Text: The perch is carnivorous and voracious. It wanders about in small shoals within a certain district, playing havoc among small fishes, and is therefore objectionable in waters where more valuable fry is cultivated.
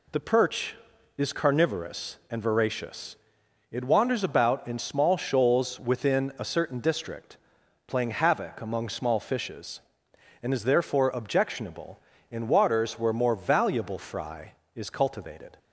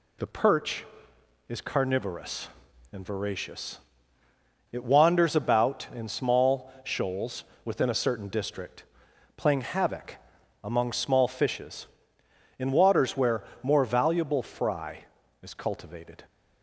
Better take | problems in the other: first | pauses between "shoals" and "within"; slight; at 7.4 s; 0.22 s long // pauses between "havoc" and "among"; noticeable; at 10.1 s; 0.48 s long // skips "and is therefore objectionable"; at 12.2 s // pauses between "where" and "more"; slight; at 13.4 s; 0.18 s long

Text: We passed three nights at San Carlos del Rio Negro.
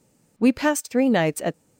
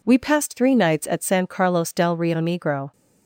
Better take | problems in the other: second | stops before "San Carlos del Rio Negro"; at 1.5 s

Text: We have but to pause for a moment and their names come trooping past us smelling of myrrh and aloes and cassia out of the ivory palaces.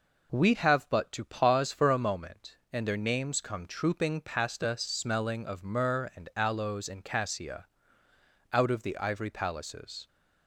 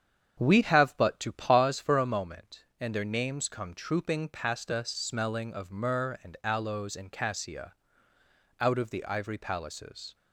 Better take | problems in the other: first | starts louder than the rest; strong; until 1.7 s; 8 dB // pauses between "cassia" and "out"; noticeable; at 7.7 s; 0.86 s long; noticeable in the first

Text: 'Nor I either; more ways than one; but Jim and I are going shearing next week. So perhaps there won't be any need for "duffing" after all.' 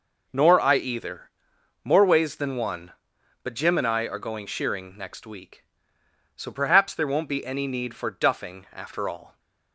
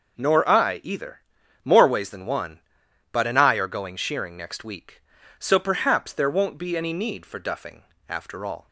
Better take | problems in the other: first | skips "Jim"; at 3.2 s // pauses between "duffing" and "after"; slight; at 7.8 s; 0.26 s long

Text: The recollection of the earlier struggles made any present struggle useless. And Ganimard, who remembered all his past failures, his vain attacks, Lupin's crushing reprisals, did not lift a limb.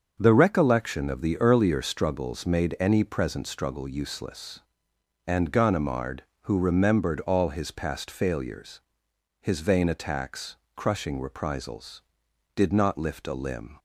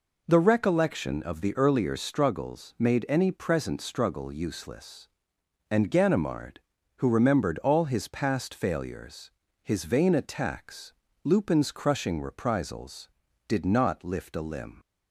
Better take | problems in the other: second | starts louder than the rest; until 1.2 s; 6.5 dB // skips "Lupin's"; at 10.6 s

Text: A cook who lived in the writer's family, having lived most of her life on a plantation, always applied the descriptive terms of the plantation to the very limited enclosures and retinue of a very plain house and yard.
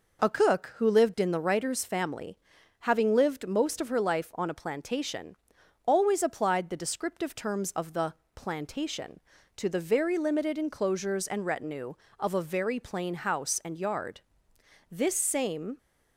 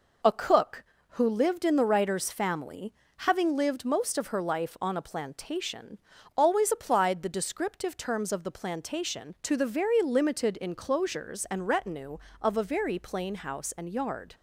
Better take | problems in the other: second | pauses between "the" and "plantation"; slight; at 8.1 s; 0.20 s long // goes on to say "This same"; noticeable; from 14.8 s on; 0.88 s long

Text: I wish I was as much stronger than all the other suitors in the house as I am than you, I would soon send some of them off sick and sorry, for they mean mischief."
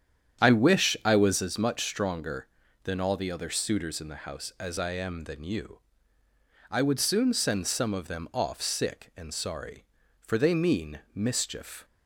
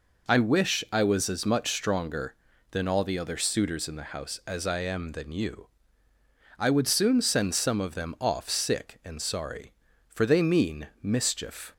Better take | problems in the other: second | starts louder than the rest; strong; until 1.6 s; 9 dB

